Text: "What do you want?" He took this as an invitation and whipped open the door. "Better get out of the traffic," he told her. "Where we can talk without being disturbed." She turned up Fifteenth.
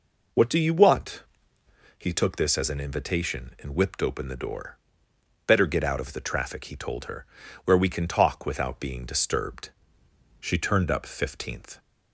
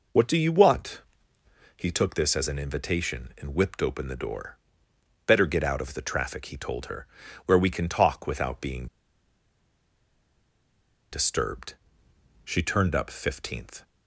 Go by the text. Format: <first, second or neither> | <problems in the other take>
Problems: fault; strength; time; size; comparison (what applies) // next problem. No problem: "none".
first | pauses between "being" and "disturbed"; strong; at 8.8 s; 2.2 s long